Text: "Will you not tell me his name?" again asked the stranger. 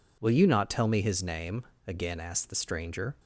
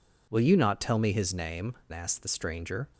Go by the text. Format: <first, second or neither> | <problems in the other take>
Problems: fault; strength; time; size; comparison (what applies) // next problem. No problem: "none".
first | skips "again"; at 1.8 s